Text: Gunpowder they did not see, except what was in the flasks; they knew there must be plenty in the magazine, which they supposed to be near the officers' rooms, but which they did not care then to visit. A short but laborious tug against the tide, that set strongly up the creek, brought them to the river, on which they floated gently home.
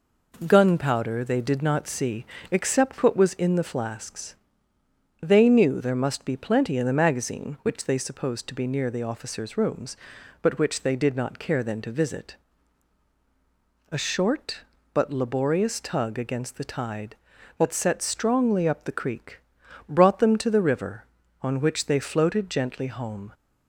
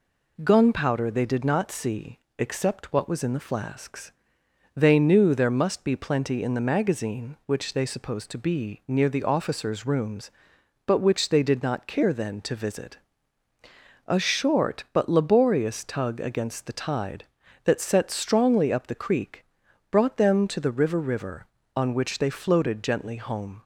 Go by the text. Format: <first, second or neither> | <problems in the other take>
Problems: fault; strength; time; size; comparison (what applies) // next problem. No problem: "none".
first | says "river" twice; at 20.9 s